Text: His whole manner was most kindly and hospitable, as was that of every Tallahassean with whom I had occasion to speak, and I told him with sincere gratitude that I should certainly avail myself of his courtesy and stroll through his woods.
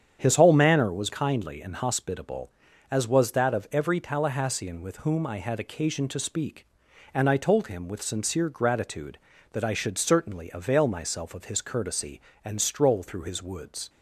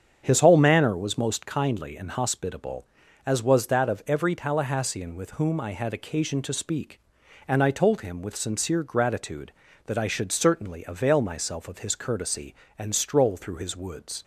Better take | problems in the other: second | starts louder than the rest; strong; until 1.2 s; 8.5 dB; strong in the second // skips "most"; at 1.1 s

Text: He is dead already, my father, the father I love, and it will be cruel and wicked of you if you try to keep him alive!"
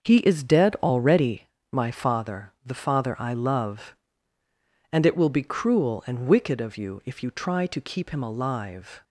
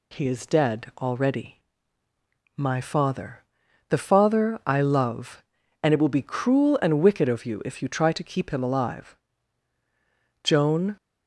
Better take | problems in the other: first | goes on to say "Joan"; from 10.4 s on; 0.54 s long

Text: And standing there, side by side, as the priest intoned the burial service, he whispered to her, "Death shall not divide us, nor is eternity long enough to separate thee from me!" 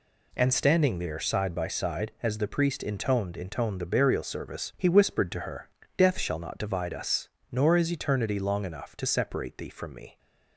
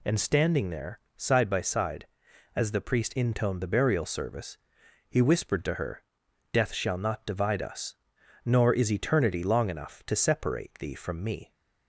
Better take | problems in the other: second | says "intoned" twice; at 3.3 s

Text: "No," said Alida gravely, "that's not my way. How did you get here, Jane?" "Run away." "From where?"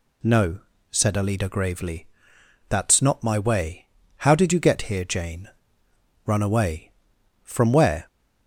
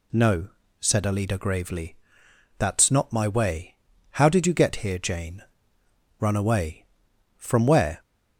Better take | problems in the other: neither | none

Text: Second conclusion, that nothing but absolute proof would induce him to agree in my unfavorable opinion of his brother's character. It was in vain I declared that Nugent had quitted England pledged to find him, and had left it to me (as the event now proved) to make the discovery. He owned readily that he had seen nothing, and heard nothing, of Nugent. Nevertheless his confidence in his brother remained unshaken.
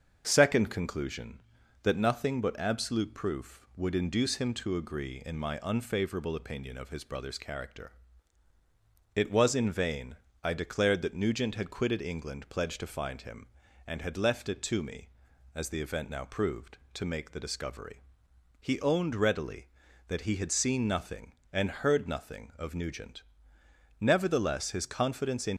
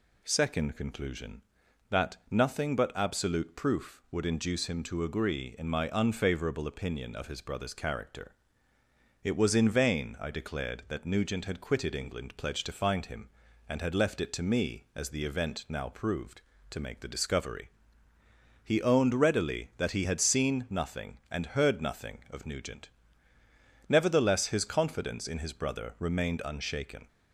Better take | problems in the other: second | starts louder than the rest; until 1.2 s; 6.5 dB // pauses between "vain" and "I"; slight; at 10.1 s; 0.26 s long // stops before "his brother remained unshaken"; at 25.5 s

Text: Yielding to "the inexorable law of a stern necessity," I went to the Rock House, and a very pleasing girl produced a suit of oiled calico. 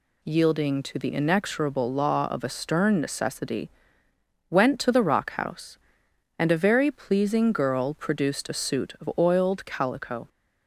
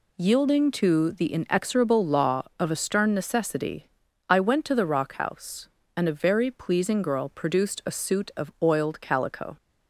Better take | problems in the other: second | skips "I"; at 4.1 s

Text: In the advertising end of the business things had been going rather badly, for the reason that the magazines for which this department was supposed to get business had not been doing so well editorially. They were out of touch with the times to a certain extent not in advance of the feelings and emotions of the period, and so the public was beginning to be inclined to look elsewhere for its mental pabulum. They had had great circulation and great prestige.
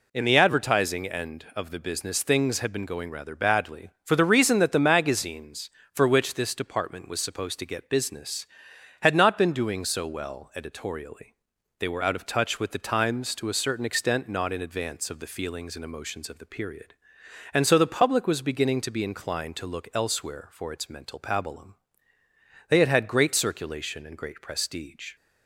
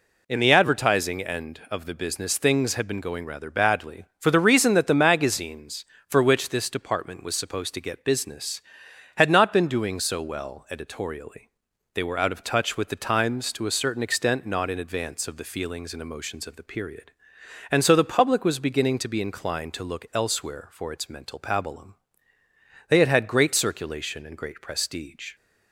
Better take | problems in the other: neither | none

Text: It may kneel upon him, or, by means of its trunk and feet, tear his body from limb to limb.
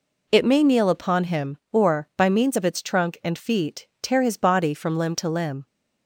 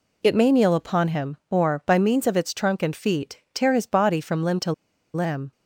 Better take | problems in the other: first | pauses between "to" and "limb"; at 4.7 s; 0.42 s long

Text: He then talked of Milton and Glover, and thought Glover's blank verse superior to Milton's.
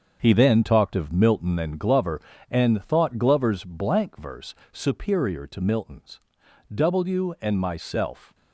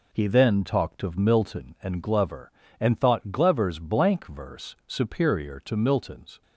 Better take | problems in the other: second | starts louder than the rest; until 1.2 s; 6.5 dB // pauses between "verse" and "superior"; slight; at 4.5 s; 0.16 s long // goes on to say "W and myself"; from 6.7 s on; 1.6 s long

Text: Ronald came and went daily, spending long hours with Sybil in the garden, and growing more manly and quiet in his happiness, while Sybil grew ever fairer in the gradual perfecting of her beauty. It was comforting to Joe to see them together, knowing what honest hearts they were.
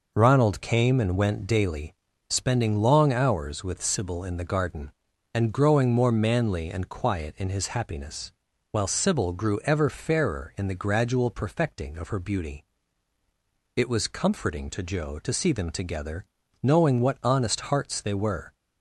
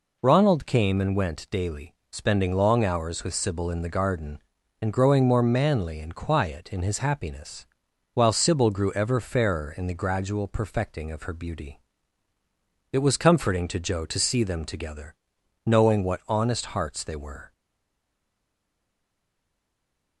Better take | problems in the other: first | stays silent after the last word; strong; from 17.5 s on; 2.7 s long

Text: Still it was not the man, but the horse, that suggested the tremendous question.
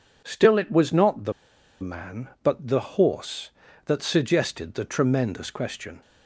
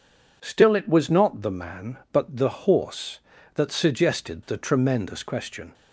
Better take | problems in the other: second | pauses between "the" and "man"; noticeable; at 1.3 s; 0.48 s long

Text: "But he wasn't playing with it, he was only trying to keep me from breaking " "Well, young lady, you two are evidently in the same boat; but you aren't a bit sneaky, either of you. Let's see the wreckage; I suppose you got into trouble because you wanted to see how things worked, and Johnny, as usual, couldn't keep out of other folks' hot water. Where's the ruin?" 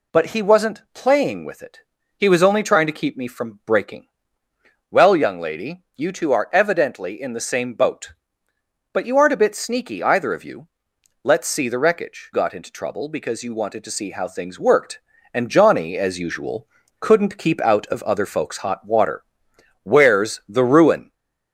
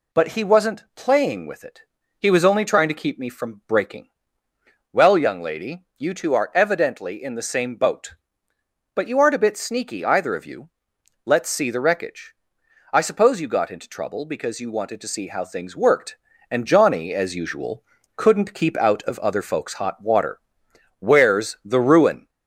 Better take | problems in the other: second | skips "I suppose you"; at 12.3 s

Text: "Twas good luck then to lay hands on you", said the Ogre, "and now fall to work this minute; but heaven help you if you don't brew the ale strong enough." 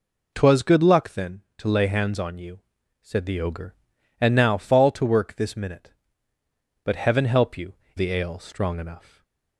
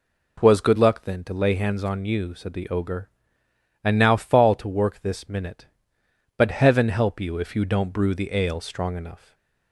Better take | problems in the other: second | skips "if you don't brew"; at 7.8 s // stays silent after the last word; slight; from 8.9 s on; 0.6 s long; slight in the second

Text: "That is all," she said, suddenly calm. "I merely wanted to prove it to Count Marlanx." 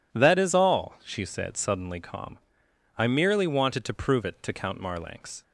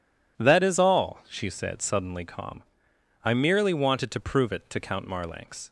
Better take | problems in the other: neither | none

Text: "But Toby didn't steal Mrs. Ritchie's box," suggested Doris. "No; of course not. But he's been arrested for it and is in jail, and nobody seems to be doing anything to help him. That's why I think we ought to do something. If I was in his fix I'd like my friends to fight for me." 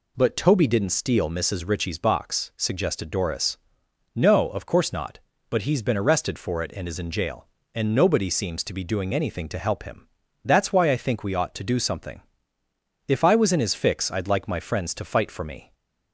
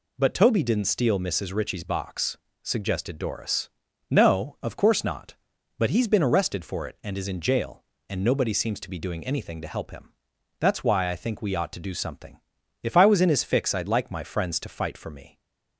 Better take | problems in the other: neither | none

